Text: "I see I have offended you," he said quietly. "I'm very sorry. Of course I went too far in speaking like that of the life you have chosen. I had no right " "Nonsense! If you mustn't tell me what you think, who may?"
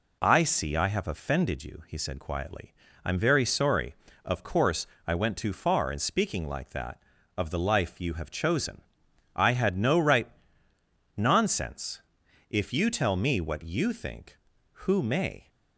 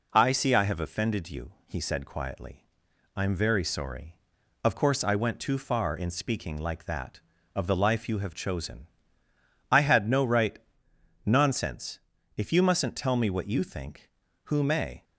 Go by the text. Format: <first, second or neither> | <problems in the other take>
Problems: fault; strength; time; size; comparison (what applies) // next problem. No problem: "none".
second | pauses between "course" and "I"; slight; at 4.8 s; 0.20 s long // skips "mustn't"; at 12.8 s